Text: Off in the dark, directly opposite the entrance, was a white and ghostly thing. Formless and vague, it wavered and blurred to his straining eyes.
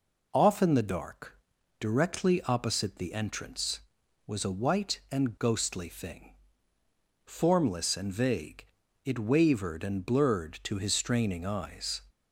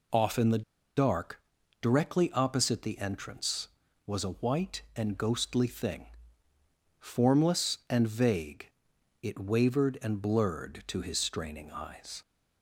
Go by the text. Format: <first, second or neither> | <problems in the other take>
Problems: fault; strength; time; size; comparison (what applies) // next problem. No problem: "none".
first | pauses between "the" and "dark"; slight; at 0.6 s; 0.34 s long